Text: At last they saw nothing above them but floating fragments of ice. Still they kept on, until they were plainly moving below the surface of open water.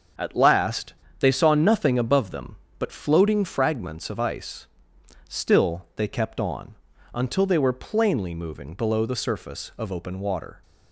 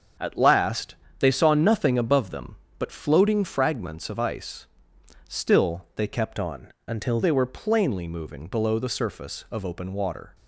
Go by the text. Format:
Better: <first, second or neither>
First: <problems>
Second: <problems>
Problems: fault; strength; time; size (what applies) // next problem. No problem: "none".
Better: first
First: starts louder than the rest; until 1.4 s; 6.5 dB // pauses between "last" and "they"; slight; at 0.9 s; 0.26 s long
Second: starts louder than the rest; until 1.4 s; 7 dB // pauses between "last" and "they"; slight; at 0.9 s; 0.24 s long // changes voice from "on" to "until"; from 6.3 to 7.2 s; 0.9 s long